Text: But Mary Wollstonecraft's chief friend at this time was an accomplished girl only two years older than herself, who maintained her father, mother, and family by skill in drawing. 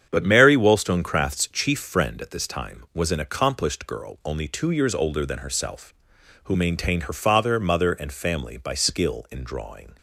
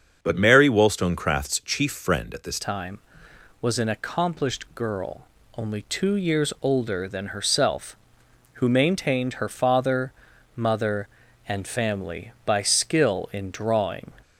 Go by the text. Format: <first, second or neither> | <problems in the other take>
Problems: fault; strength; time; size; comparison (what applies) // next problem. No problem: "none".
first | starts louder than the rest; until 1.2 s; 7 dB; strong in the first // changes voice at "time"; from 2.5 s on; 11.6 s long // pauses between "girl" and "only"; slight; at 5.2 s; 0.30 s long